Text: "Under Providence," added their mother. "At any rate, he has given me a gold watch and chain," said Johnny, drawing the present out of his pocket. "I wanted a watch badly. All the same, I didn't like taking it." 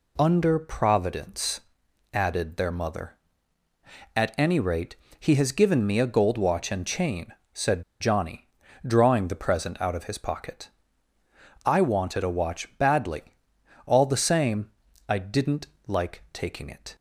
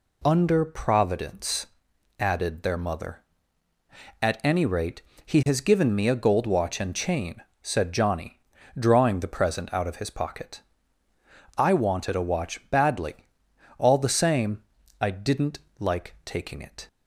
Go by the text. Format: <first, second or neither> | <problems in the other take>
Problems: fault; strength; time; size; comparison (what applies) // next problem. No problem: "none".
second | pauses between "said" and "Johnny"; slight; at 7.8 s; 0.17 s long // pauses between "didn't" and "like"; slight; at 15.6 s; 0.20 s long; slight in the second